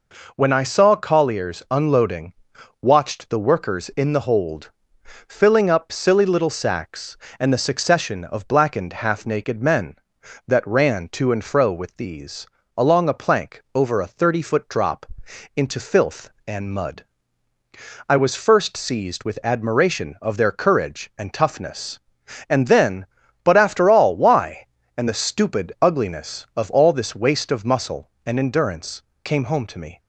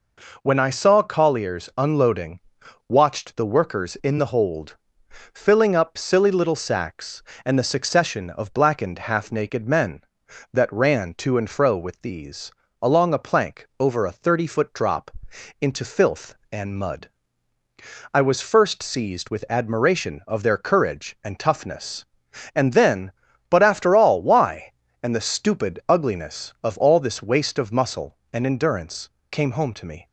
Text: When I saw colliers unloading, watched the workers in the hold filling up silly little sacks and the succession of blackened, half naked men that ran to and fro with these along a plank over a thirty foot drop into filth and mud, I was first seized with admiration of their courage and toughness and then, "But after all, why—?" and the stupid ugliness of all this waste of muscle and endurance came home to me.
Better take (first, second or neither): neither